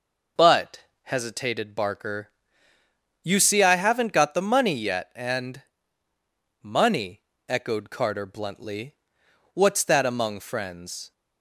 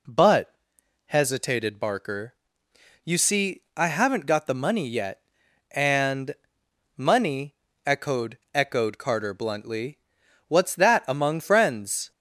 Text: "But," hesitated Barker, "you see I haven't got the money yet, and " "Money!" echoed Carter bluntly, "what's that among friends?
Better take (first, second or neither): first